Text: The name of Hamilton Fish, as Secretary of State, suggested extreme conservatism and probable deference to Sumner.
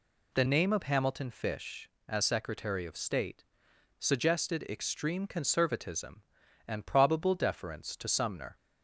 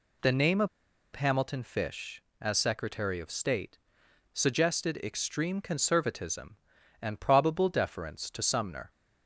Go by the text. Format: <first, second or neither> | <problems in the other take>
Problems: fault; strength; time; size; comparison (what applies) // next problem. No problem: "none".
first | pauses between "of" and "Hamilton"; noticeable; at 0.6 s; 0.47 s long